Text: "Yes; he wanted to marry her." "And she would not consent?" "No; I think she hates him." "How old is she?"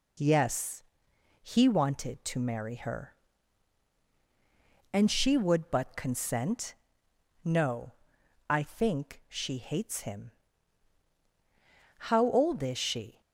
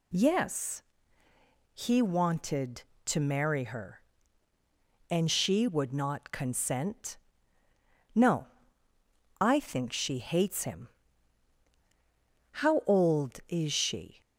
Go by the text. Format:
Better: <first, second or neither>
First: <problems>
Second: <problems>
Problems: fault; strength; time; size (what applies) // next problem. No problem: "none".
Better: second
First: says "but" for "not"; at 5.7 s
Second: none